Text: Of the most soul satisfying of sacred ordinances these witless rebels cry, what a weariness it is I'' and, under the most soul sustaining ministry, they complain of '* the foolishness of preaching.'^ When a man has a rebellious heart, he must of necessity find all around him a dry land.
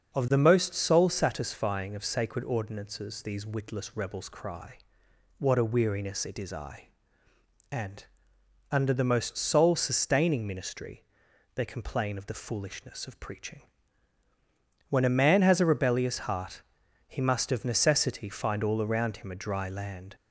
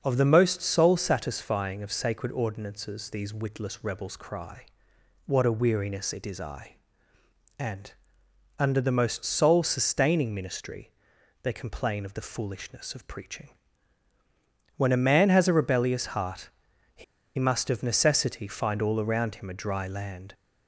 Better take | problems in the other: first | starts louder than the rest; until 1.0 s; 6 dB; also in the first // pauses between "he" and "must"; slight; at 17.0 s; 0.33 s long

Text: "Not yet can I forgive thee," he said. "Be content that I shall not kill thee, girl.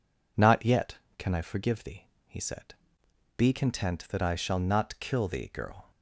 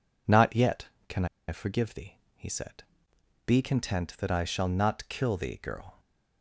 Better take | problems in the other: first | pauses between "can" and "I"; slight; at 1.2 s; 0.23 s long

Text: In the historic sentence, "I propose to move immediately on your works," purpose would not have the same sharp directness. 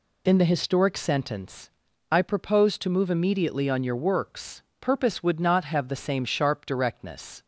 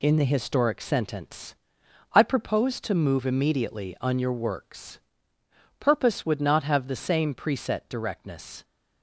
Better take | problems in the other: first | says "preset" for "sharp"; at 7.3 s

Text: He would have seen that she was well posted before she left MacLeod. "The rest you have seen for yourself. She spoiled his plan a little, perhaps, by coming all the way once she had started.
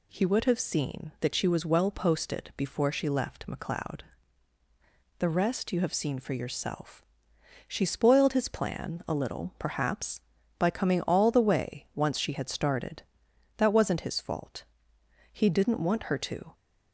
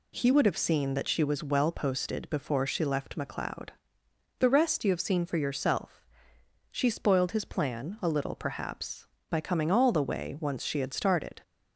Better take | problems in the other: second | goes on to say "That wasn't his fault he didn't want her to"; strong; from 13.5 s on; 2.9 s long

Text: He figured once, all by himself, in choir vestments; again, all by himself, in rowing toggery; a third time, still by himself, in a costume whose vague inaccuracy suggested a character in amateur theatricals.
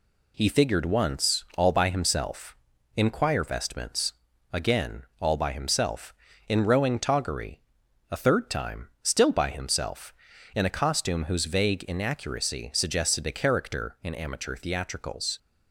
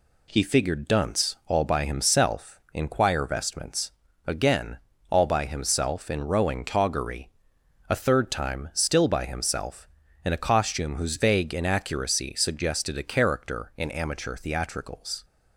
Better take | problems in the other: first | says "dunce" for "once"; at 0.8 s

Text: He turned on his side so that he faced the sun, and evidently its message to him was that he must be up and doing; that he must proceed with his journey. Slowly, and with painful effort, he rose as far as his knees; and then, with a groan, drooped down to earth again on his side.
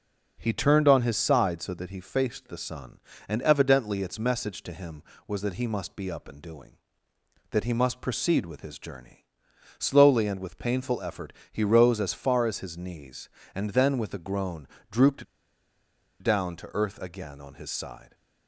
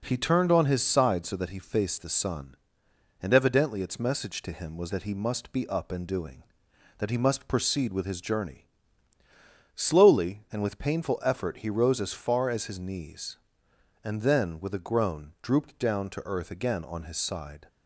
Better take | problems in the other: second | pauses between "drooped" and "down"; noticeable; at 15.2 s; 0.97 s long

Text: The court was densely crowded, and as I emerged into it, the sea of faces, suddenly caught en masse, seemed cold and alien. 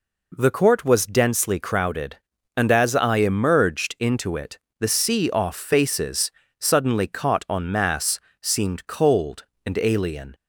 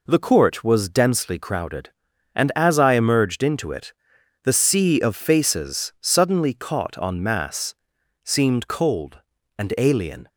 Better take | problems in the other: second | says "off" for "of"; at 5.3 s

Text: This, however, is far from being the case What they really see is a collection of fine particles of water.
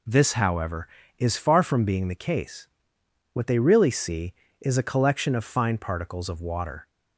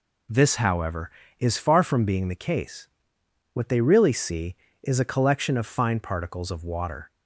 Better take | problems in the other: neither | pauses between "case" and "What"; noticeable; the same in both

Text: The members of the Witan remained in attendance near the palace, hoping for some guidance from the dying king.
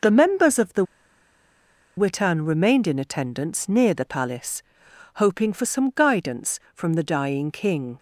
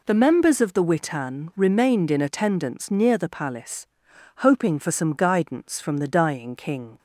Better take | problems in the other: second | pauses between "the" and "Witan"; at 0.8 s; 1.1 s long

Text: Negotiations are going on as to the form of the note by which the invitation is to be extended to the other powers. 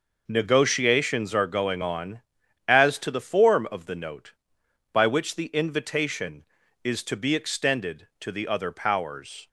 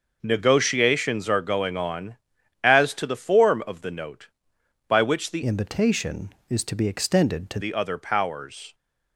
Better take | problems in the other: first | changes voice from "invitation" to "to"; from 5.4 to 7.5 s; 2.1 s long

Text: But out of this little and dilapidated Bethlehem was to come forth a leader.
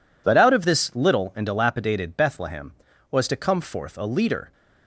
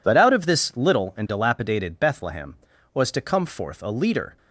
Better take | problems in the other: neither | none

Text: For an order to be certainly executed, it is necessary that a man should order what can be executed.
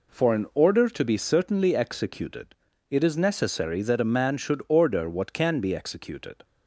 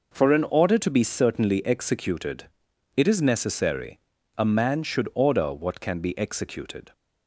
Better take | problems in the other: first | skips "that"; at 4.1 s

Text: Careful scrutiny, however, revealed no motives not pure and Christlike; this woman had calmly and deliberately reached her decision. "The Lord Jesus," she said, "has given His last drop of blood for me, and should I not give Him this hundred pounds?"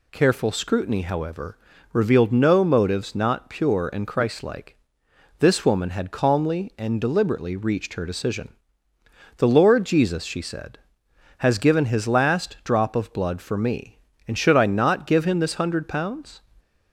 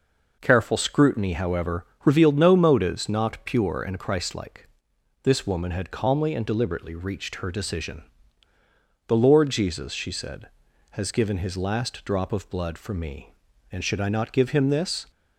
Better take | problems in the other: first | stops before "hundred pounds"; at 15.1 s

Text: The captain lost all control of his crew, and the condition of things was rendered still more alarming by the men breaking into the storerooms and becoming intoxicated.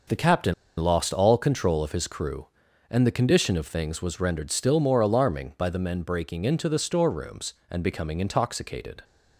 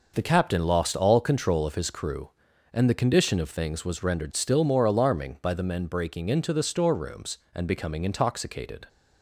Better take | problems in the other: second | starts louder than the rest; noticeable; until 1.3 s; 6 dB // pauses between "captain" and "lost"; slight; at 0.5 s; 0.25 s long

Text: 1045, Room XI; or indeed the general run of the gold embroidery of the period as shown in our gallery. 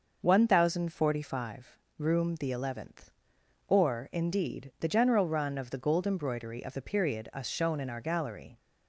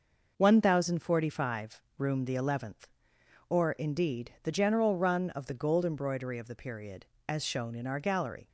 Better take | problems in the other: second | says "us" for "as"; at 7.3 s

